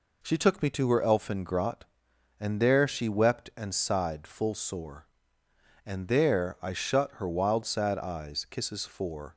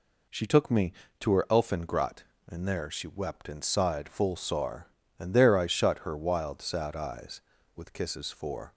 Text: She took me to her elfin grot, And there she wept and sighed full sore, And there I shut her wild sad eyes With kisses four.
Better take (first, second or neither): second